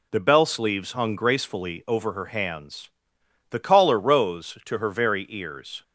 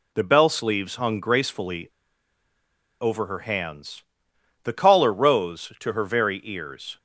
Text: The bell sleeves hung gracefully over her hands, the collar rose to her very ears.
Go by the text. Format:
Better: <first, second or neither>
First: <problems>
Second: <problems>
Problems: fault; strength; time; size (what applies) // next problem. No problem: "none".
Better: first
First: none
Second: pauses between "gracefully" and "over"; at 1.8 s; 1.1 s long